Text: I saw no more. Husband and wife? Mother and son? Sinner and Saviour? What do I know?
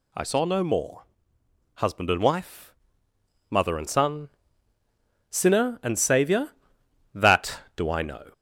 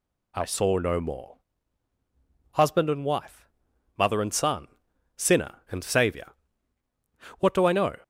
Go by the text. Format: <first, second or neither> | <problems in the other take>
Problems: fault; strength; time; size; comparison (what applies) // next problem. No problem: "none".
second | says "That" for "What"; at 7.1 s